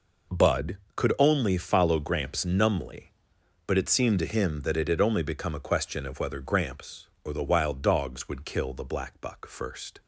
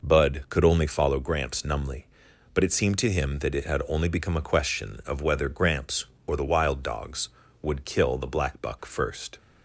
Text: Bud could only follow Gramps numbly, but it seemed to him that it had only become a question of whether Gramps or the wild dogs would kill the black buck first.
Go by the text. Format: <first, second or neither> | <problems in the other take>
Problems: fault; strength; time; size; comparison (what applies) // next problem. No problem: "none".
neither | none